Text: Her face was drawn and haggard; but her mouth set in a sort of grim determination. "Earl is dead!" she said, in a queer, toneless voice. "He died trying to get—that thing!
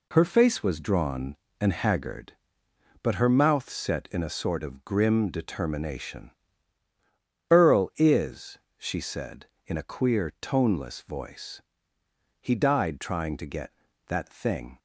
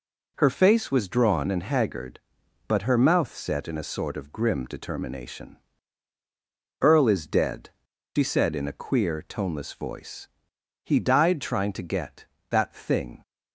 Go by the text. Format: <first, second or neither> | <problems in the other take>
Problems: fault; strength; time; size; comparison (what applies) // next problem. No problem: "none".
second | skips "dead"; at 8.6 s